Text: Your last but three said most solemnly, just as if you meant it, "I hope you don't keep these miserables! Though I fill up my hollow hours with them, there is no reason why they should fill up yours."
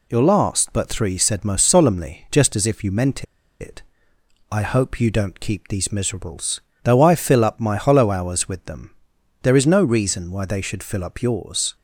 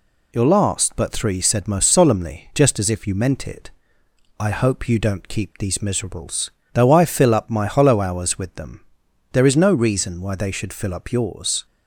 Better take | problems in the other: second | pauses between "meant" and "it"; at 3.2 s; 0.36 s long

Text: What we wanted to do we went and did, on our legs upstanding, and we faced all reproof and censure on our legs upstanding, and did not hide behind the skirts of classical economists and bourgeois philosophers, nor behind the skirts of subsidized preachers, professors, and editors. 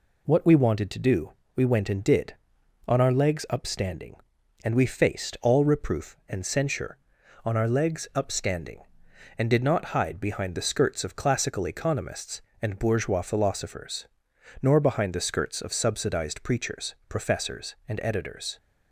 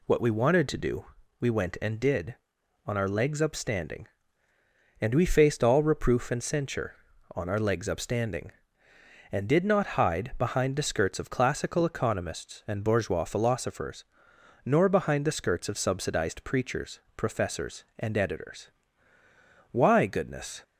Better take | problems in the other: first | pauses between "do" and "we"; slight; at 1.0 s; 0.34 s long; slight in the first // goes on to say "Why goodness"; noticeable; from 19.7 s on; 0.92 s long

